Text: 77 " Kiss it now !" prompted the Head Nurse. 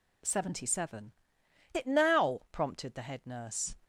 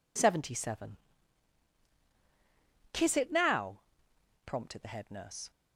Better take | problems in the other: second | skips "Kiss"; at 1.7 s

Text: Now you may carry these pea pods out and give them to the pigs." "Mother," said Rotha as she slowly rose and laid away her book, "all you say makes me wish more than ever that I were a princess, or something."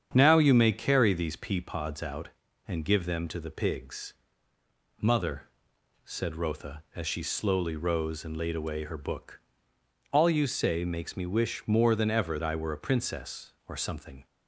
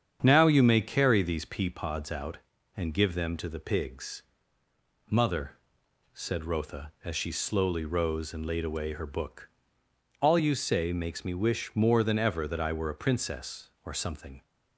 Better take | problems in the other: second | starts louder than the rest; strong; until 1.1 s; 8 dB; strong in the second // skips "that"; at 12.4 s

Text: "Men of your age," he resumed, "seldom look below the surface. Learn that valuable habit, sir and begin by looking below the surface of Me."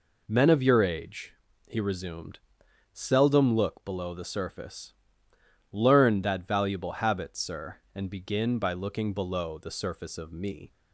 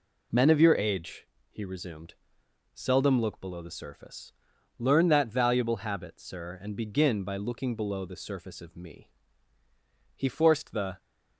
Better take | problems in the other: first | goes on to say "He forced the"; noticeable; from 10.1 s on; 0.84 s long

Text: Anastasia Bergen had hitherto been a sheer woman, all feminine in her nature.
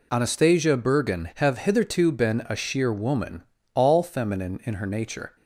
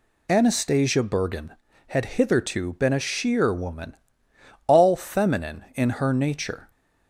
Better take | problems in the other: second | says "have" for "had"; at 1.3 s

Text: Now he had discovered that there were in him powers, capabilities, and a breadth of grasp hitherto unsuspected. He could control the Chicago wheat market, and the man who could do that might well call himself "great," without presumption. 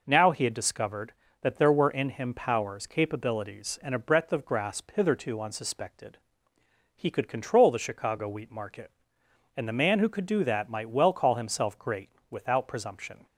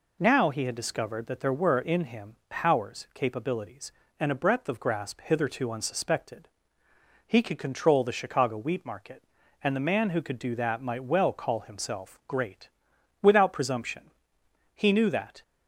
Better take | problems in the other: first | goes on to say "He knew that"; noticeable; from 14.7 s on; 0.68 s long

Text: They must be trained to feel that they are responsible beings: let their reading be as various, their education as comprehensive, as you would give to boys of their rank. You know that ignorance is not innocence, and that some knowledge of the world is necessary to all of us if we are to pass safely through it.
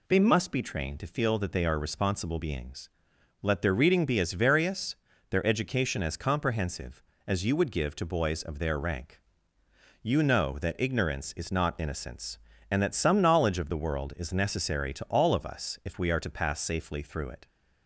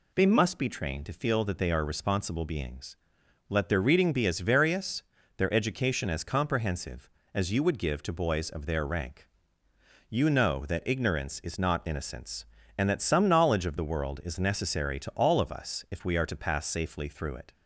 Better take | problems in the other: neither | none

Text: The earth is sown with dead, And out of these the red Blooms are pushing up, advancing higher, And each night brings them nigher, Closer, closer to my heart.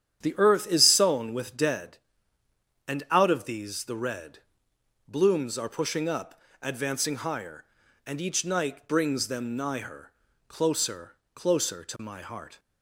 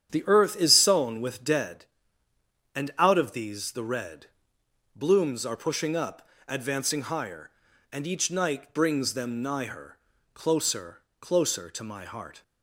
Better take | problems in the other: neither | starts louder than the rest; strong; the same in both // pauses between "red" and "Blooms"; noticeable; the same in both

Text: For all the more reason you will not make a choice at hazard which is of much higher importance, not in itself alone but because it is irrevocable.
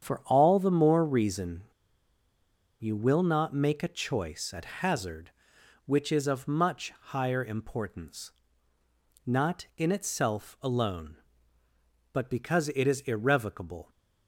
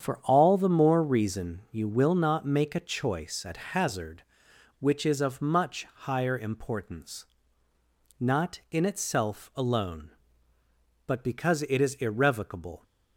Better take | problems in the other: second | starts louder than the rest; strong; until 1.0 s; 8 dB; strong in the second // pauses between "reason" and "you"; at 1.6 s; 1.1 s long

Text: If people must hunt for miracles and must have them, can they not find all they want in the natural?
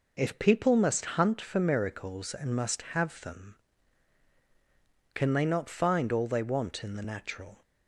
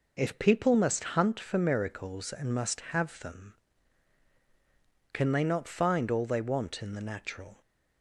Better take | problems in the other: neither | none

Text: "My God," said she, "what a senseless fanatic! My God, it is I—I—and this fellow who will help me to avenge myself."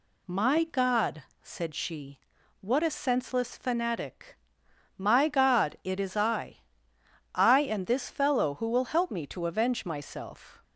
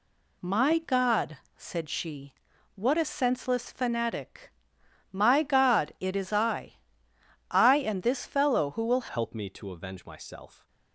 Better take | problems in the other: first | changes voice at "help"; from 9.0 s on; 1.6 s long

